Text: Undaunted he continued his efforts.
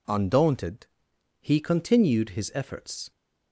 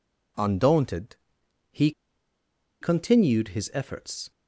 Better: first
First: pauses between "Undaunted" and "he"; noticeable; at 0.8 s; 0.53 s long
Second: pauses between "Undaunted" and "he"; noticeable; at 1.1 s; 0.54 s long // pauses between "he" and "continued"; noticeable; at 1.9 s; 0.91 s long

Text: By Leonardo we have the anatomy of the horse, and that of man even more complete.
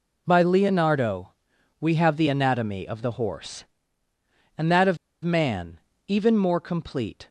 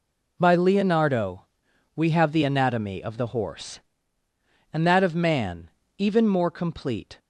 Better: second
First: pauses between "Leonardo" and "we"; noticeable; at 1.3 s; 0.46 s long // pauses between "of" and "man"; slight; at 4.9 s; 0.26 s long // pauses between "man" and "even"; slight; at 5.7 s; 0.30 s long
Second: pauses between "Leonardo" and "we"; noticeable; at 1.4 s; 0.48 s long // pauses between "man" and "even"; slight; at 5.6 s; 0.30 s long

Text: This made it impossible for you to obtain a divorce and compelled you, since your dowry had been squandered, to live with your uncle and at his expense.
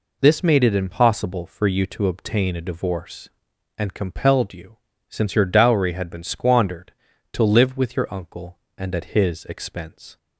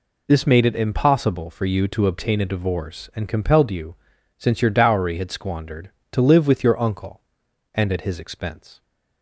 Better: first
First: none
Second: skips "been"; at 5.3 s

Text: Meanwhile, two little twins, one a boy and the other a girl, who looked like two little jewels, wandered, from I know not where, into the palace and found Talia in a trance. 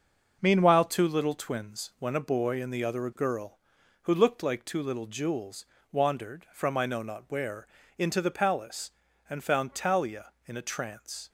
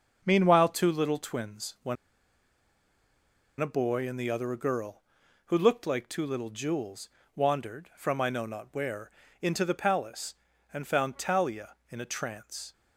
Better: first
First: none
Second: pauses between "one" and "a"; strong; at 1.9 s; 1.6 s long

